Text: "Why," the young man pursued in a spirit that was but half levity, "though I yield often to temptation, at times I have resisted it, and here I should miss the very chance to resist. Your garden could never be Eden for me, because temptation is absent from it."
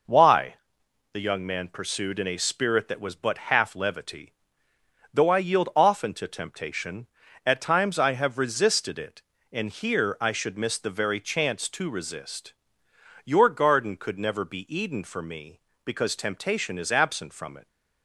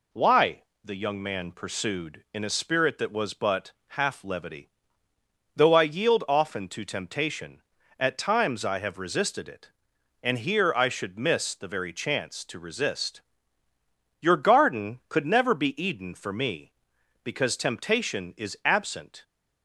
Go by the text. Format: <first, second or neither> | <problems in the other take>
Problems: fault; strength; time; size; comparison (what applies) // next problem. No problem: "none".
first | pauses between "but" and "half"; slight; at 3.7 s; 0.20 s long // stops before "from it"; at 19.2 s